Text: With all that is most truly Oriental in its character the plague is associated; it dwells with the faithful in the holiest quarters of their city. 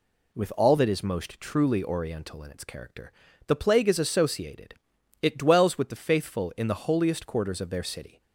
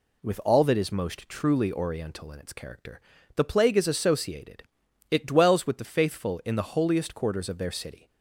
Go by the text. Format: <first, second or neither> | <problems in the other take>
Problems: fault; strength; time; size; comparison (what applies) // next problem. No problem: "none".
neither | pauses between "character" and "the"; slight; the same in both